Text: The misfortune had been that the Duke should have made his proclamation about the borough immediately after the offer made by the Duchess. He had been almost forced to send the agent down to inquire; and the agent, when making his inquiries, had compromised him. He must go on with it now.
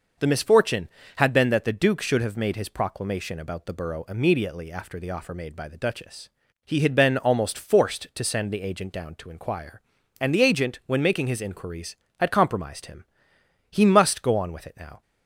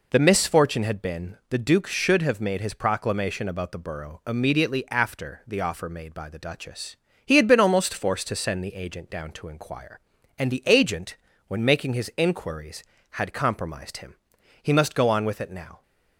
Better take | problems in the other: first | skips "that"; at 1.4 s

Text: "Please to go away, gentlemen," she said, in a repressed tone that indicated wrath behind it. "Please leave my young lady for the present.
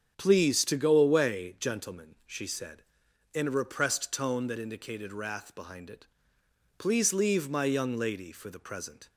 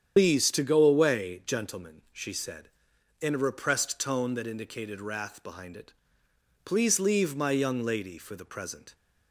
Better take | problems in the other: first | loses the start of "Please"; at 0.1 s; 135 ms // starts louder than the rest; strong; until 1.1 s; 8.5 dB; strong in the first

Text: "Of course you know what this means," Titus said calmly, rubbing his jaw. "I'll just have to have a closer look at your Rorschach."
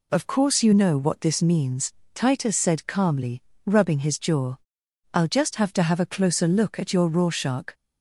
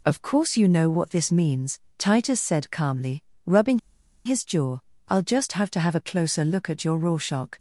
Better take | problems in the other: first | pauses between "rubbing" and "his"; noticeable; at 3.7 s; 0.46 s long

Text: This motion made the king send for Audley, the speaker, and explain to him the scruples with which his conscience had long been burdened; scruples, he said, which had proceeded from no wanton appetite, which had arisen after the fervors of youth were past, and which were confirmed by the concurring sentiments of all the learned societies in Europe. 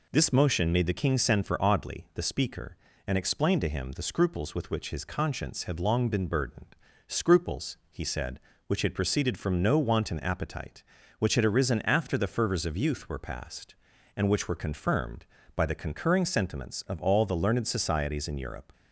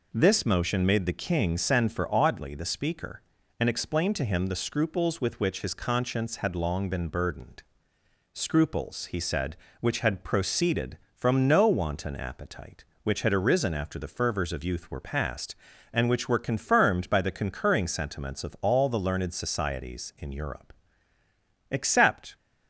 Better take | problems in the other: first | goes on to say "Except"; noticeable; from 21.6 s on; 0.64 s long

